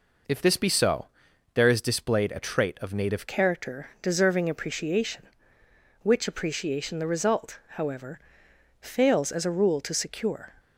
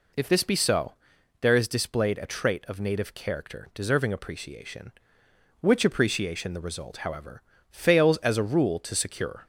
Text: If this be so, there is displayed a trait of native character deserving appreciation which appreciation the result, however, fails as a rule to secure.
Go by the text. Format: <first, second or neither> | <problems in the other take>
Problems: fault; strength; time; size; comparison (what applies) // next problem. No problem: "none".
second | changes voice at "character"; from 3.2 s on; 7.3 s long